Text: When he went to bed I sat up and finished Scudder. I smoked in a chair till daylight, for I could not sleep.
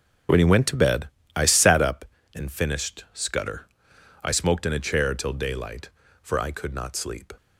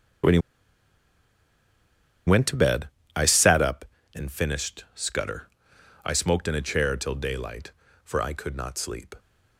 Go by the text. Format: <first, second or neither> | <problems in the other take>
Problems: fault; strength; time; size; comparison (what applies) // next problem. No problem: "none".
first | starts louder than the rest; strong; until 3.3 s; 7.5 dB; strong in the first // pauses between "he" and "went"; strong; at 0.3 s; 1.8 s long // pauses between "bed" and "I"; slight; at 2.8 s; 0.26 s long; slight in the first